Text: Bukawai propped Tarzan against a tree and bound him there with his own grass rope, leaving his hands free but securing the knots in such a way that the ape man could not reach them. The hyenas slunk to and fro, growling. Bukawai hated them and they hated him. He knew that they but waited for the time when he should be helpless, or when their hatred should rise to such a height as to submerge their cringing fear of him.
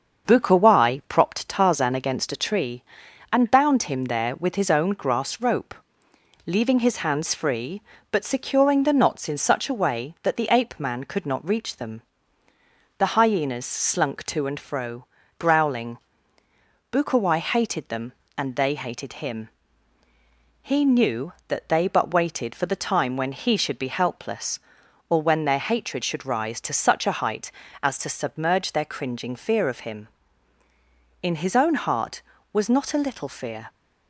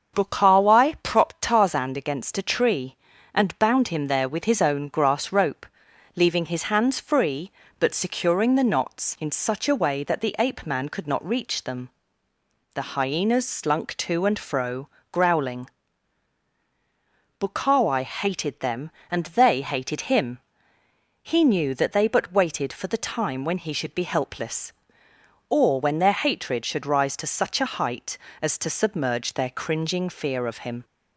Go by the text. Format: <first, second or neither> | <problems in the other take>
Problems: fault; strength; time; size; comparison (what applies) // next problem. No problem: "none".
second | starts louder than the rest; until 1.3 s; 7 dB; strong in the second // goes on to say "In his own heart was not a little fear"; strong; from 31.2 s on; 2.4 s long